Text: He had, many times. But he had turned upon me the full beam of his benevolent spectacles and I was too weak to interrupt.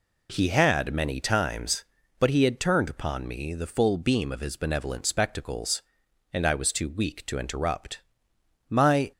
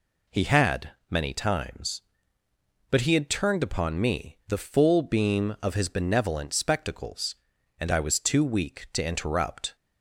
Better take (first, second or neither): second